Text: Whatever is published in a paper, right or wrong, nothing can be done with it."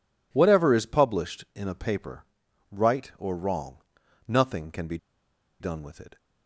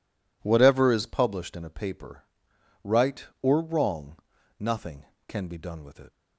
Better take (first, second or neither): second